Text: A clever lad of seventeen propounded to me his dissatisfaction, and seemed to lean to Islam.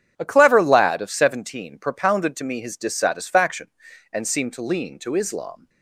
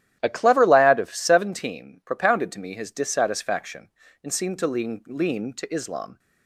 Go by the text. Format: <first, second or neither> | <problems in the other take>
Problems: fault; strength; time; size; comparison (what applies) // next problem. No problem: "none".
first | starts louder than the rest; strong; until 1.2 s; 12.5 dB; strong in the first // says "lean" twice; at 5.0 s